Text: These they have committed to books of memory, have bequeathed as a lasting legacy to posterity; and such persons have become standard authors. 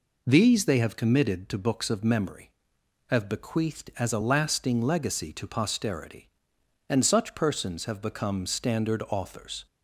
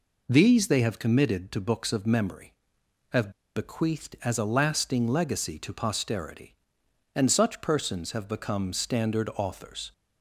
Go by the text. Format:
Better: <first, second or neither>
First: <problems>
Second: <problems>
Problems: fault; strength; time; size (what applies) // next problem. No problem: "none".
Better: first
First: none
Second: pauses between "have" and "bequeathed"; slight; at 3.3 s; 0.24 s long